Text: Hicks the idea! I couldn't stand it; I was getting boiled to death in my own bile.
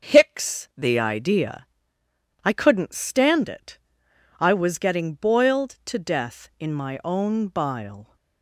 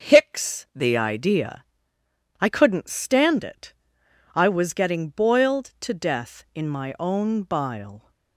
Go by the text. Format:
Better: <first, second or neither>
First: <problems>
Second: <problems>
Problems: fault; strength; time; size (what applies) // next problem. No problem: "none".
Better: neither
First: starts louder than the rest; until 1.1 s; 6.5 dB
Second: starts louder than the rest; until 1.1 s; 7 dB